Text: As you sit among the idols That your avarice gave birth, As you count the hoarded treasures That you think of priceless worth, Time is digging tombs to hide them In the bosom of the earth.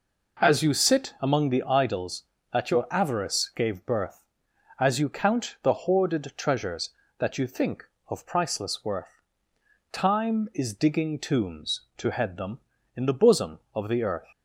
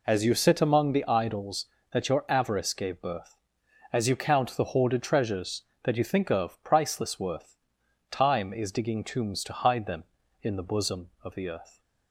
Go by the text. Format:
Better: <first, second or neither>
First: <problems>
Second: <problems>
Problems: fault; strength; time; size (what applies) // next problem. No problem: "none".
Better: second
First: says "head" for "hide"; at 12.1 s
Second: none